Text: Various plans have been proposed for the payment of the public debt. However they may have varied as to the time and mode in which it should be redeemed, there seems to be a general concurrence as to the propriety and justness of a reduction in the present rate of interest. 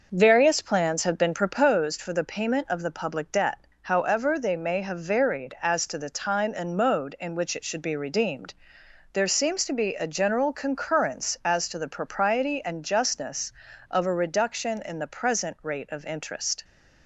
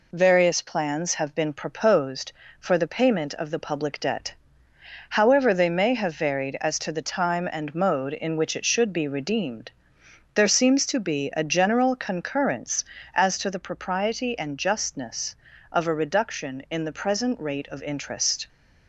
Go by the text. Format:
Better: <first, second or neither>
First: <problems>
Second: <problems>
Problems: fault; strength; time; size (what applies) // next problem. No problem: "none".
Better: second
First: starts louder than the rest; noticeable; until 1.9 s; 6 dB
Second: none